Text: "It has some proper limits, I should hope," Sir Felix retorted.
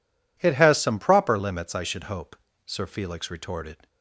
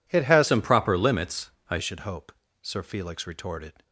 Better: first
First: none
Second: changes voice from "some" to "I"; from 0.4 to 1.7 s; 1.3 s long

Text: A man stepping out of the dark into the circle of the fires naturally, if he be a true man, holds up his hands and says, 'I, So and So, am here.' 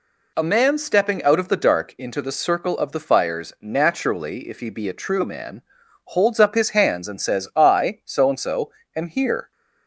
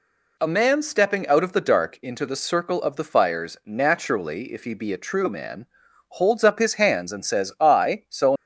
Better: first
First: none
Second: stops before "and So am here"; at 8.3 s

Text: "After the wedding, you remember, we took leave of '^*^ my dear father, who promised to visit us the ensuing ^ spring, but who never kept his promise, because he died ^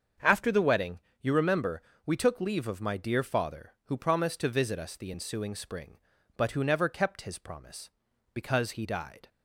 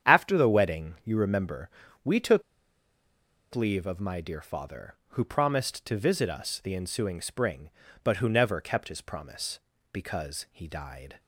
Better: first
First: starts louder than the rest; until 1.4 s; 7 dB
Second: starts louder than the rest; strong; until 1.1 s; 9 dB // pauses between "took" and "leave"; at 2.4 s; 1.1 s long

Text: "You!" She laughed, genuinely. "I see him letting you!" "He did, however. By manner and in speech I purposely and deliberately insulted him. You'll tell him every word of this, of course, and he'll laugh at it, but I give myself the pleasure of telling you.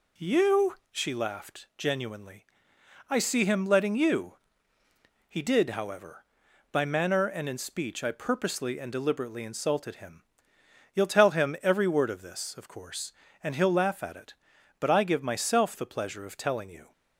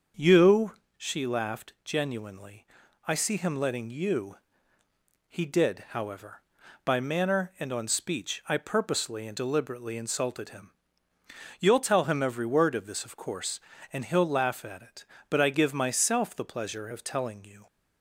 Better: first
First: none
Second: starts louder than the rest; until 1.3 s; 6.5 dB // says "on" for "in"; at 7.7 s

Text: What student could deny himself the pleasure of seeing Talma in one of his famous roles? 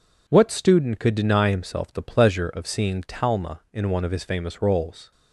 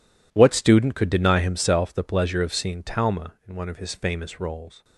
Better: first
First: none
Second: gets quieter; strong; throughout; 14 dB

